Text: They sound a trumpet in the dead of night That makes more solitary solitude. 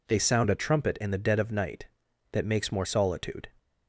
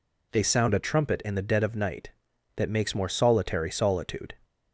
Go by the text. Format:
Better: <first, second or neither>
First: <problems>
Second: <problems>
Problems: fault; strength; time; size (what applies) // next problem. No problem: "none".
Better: second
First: skips "solitary"; at 2.8 s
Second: none